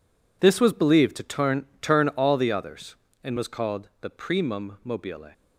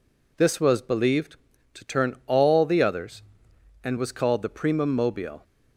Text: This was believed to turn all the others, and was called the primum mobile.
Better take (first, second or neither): second